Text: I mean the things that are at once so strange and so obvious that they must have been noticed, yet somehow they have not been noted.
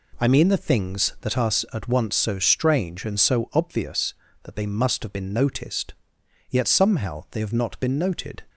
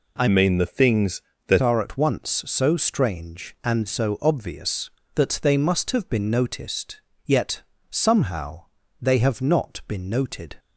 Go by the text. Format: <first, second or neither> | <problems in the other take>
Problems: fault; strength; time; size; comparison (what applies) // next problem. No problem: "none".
first | changes voice from "mean" to "that"; from 0.2 to 1.6 s; 1.4 s long // pauses between "yet" and "somehow"; slight; at 7.6 s; 0.30 s long // pauses between "somehow" and "they"; slight; at 8.6 s; 0.34 s long